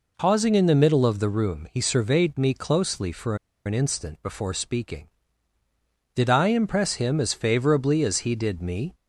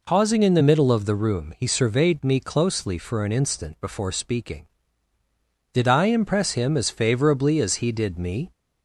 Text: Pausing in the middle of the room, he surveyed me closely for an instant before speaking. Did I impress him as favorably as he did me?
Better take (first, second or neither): second